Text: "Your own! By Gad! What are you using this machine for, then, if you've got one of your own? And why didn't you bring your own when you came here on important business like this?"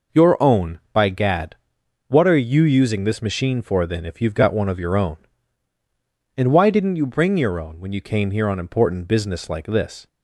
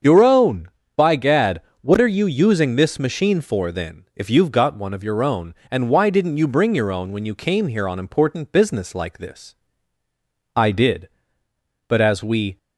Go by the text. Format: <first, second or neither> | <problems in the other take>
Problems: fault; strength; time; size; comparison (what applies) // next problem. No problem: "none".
first | starts louder than the rest; until 1.3 s; 7 dB // goes on to say "I did but as we"; strong; from 10.5 s on; 2.0 s long